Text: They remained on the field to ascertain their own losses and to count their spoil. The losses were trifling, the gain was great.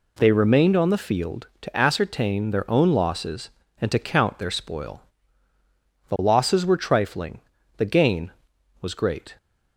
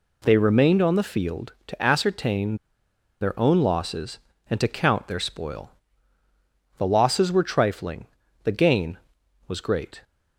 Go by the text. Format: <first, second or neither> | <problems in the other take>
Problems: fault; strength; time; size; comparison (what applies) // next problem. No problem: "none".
first | pauses between "ascertain" and "their"; noticeable; at 2.5 s; 0.66 s long